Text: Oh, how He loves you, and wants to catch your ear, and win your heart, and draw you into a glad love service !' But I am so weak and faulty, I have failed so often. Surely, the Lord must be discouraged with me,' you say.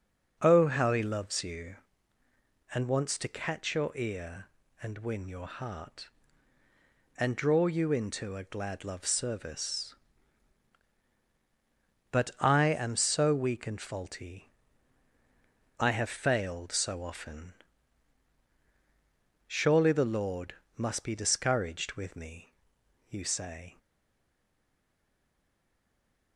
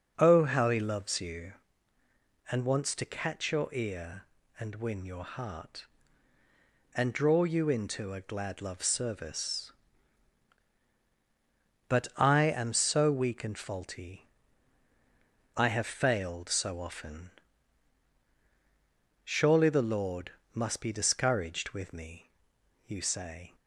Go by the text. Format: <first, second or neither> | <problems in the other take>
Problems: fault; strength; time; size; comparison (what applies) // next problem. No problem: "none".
second | starts louder than the rest; strong; until 1.4 s; 9 dB; strong in the second // pauses between "Lord" and "must"; slight; at 20.5 s; 0.24 s long; slight in the second // stays silent after the last word; strong; from 23.7 s on; 2.6 s long